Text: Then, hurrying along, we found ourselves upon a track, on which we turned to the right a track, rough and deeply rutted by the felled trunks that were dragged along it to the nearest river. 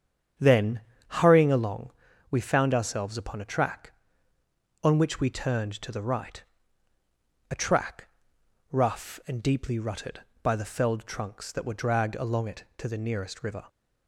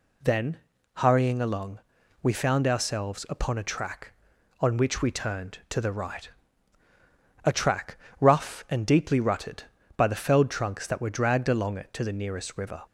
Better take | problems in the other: second | starts louder than the rest; strong; until 2.2 s; 8.5 dB // pauses between "right" and "a"; at 6.4 s; 1.0 s long; also in the second

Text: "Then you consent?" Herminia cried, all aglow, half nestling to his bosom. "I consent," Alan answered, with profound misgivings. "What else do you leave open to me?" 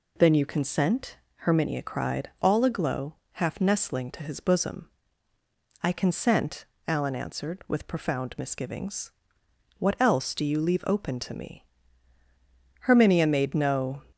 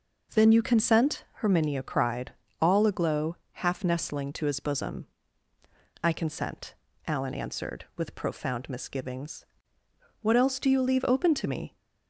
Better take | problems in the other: second | goes on to say "Herminia made no"; noticeable; from 12.8 s on; 1.2 s long

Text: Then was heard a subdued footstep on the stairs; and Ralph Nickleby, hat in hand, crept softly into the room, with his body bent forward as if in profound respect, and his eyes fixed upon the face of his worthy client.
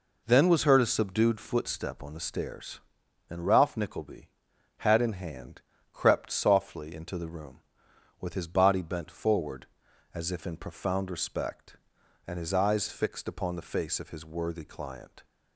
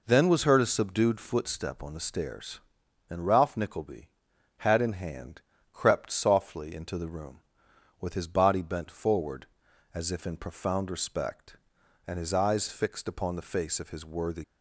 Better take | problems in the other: first | stops before "client"; at 14.4 s

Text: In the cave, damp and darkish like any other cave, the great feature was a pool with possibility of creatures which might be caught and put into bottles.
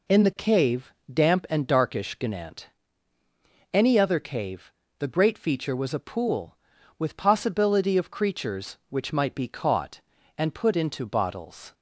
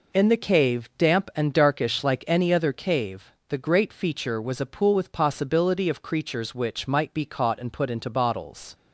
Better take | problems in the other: second | says "gnant" for "like"; at 2.1 s

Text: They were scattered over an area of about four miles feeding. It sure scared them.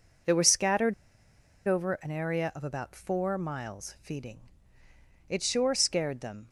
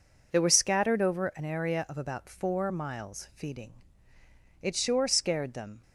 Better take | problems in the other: second | pauses between "scattered" and "over"; noticeable; at 0.9 s; 0.74 s long

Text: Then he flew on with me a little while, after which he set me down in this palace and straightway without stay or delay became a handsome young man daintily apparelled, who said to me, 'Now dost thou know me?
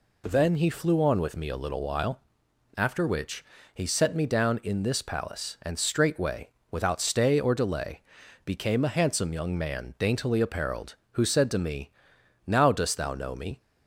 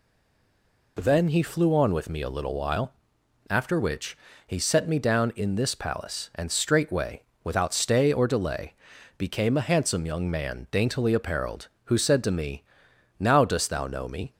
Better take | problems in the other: first | stays silent before the first word; slight; until 0.9 s; 0.9 s long // pauses between "which" and "he"; slight; at 4.1 s; 0.30 s long; slight in the first // pauses between "straightway" and "without"; slight; at 7.2 s; 0.22 s long; slight in the first // pauses between "delay" and "became"; at 8.7 s; 0.42 s long; also in the first

